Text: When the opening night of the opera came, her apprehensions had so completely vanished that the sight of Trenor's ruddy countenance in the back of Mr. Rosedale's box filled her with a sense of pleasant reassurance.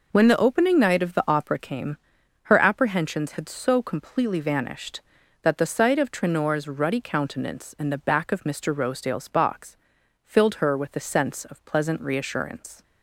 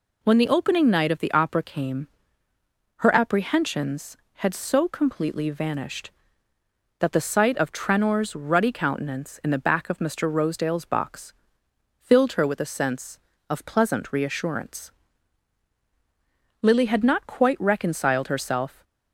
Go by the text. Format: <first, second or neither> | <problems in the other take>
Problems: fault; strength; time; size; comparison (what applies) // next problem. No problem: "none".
first | pauses between "box" and "filled"; noticeable; at 11.3 s; 0.68 s long; noticeable in the first // goes on to say "Lily had not quite reconciled herself"; strong; from 16.6 s on; 2.2 s long